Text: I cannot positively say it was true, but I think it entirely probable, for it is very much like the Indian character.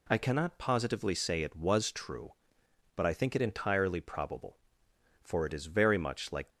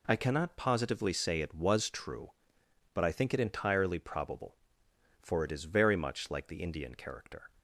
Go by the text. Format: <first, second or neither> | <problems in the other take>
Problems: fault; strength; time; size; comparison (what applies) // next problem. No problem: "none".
second | stops before "the Indian character"; at 6.4 s